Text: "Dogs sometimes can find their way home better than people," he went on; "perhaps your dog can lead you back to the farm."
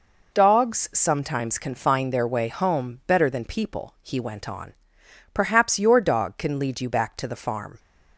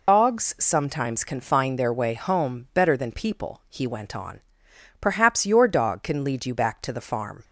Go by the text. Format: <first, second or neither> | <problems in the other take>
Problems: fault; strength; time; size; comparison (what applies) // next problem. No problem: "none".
first | loses the start of "Dogs"; at 0.0 s; 80 ms